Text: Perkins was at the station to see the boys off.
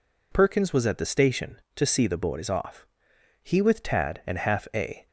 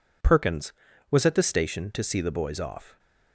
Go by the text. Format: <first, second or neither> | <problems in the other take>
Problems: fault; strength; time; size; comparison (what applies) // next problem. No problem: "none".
second | goes on to say "He with Tad and half a"; from 3.4 s on; 1.6 s long